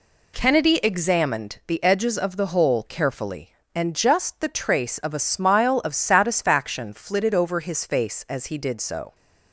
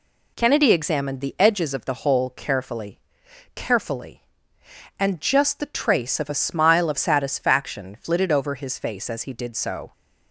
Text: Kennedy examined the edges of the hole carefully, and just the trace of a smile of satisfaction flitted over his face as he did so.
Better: first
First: none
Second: says "carefully" twice; at 3.5 s

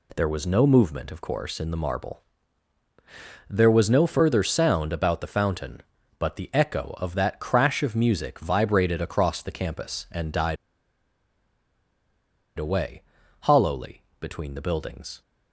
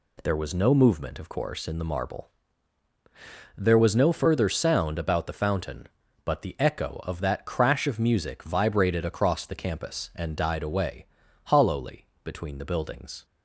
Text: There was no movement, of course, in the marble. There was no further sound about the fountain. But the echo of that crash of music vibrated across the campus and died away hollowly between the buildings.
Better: second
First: pauses between "died" and "away"; strong; at 10.5 s; 2.0 s long // pauses between "away" and "hollowly"; at 13.0 s; 0.40 s long // pauses between "hollowly" and "between"; slight; at 14.0 s; 0.16 s long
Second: pauses between "away" and "hollowly"; at 11.0 s; 0.40 s long // pauses between "hollowly" and "between"; slight; at 12.0 s; 0.16 s long

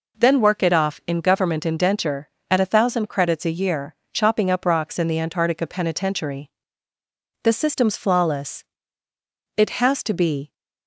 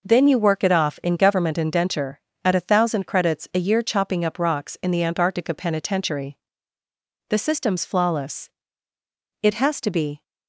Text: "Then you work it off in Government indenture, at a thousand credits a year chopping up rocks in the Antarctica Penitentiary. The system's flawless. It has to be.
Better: second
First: skips "you"; at 0.4 s // pauses between "year" and "chopping"; slight; at 3.9 s; 0.18 s long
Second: none

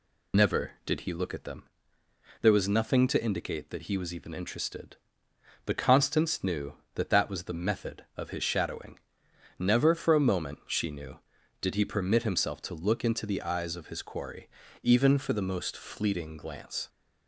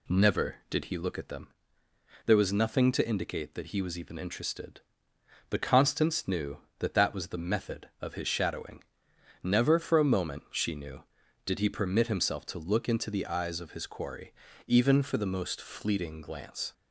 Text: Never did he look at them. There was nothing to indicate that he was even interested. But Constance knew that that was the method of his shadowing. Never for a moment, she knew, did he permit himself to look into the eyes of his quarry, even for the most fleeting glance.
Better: second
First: loses the start of "Never"; at 0.3 s; 120 ms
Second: none

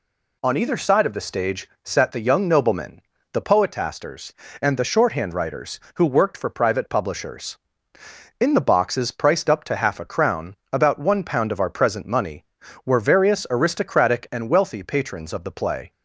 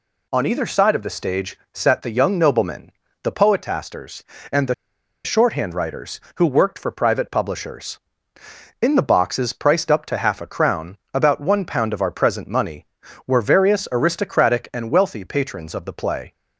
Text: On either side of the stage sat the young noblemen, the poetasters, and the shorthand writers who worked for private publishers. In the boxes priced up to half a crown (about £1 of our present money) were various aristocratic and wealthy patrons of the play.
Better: first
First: pauses between "stage" and "sat"; slight; at 1.6 s; 0.16 s long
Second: pauses between "stage" and "sat"; slight; at 1.5 s; 0.16 s long // pauses between "the" and "shorthand"; noticeable; at 4.7 s; 0.50 s long

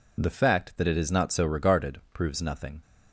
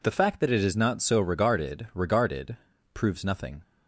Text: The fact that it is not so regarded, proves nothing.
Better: first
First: none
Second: says "regarded" twice; at 1.9 s

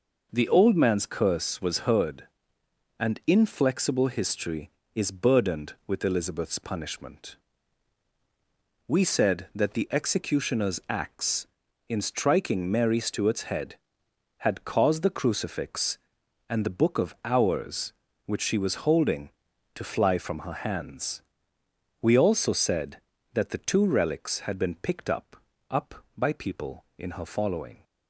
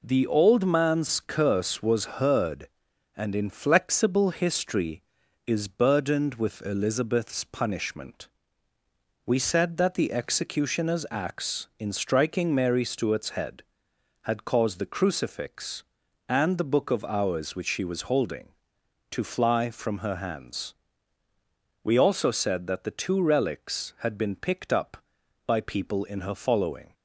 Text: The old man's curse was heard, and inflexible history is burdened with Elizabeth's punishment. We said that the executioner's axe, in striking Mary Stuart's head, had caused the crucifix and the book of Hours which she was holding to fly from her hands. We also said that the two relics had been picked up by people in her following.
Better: second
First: says "up" twice; at 25.6 s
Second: none

